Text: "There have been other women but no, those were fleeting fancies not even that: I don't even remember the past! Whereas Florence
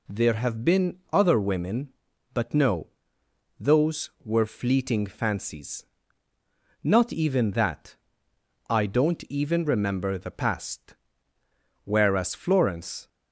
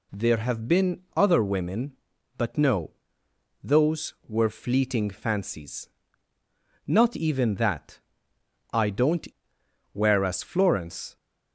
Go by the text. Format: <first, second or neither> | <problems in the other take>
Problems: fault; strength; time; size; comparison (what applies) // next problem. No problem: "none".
first | pauses between "fancies" and "not"; noticeable; at 5.9 s; 0.96 s long; noticeable in the first // skips "even remember the past"; at 9.5 s